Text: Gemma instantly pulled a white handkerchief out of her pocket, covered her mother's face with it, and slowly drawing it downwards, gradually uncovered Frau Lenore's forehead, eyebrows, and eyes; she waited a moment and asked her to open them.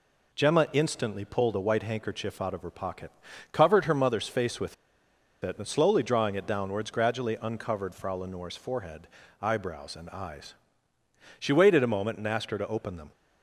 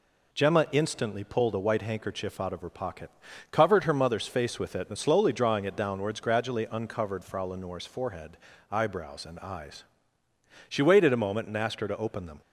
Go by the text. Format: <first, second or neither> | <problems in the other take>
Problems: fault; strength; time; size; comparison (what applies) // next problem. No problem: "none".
second | pauses between "with" and "it"; noticeable; at 4.7 s; 0.68 s long